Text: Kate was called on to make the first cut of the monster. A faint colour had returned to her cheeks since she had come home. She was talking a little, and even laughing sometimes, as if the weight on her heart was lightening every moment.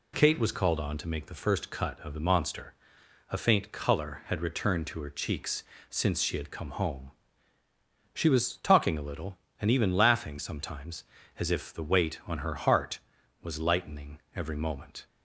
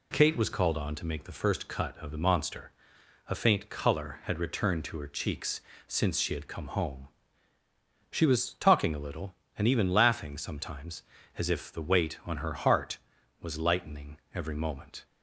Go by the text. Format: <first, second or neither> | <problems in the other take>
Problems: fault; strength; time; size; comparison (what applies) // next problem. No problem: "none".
neither | pauses between "cheeks" and "since"; slight; the same in both // pauses between "lightening" and "every"; slight; the same in both